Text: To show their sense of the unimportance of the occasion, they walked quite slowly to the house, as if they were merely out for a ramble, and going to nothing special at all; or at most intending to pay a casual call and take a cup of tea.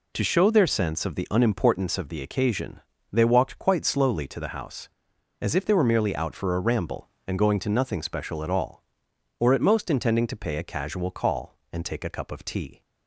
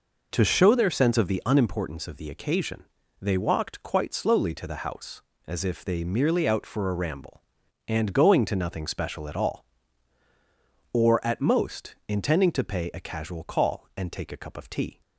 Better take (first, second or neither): first